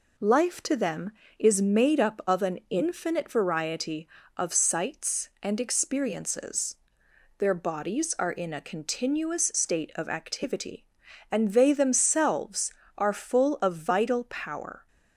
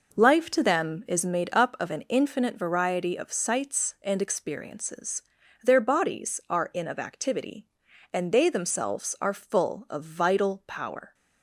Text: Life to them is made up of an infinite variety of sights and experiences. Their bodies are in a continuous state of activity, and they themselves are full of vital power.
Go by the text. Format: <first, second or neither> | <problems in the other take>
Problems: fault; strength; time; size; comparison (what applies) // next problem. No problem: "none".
first | skips "a continuous state"; at 6.8 s